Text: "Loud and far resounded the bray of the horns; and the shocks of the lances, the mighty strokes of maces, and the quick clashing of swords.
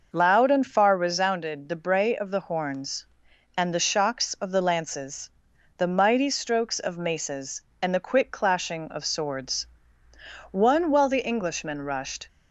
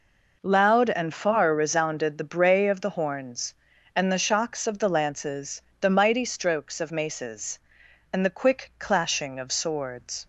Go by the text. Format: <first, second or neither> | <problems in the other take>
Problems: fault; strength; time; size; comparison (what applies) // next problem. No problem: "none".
second | goes on to say "One while the Englishmen rushed"; strong; from 10.4 s on; 1.7 s long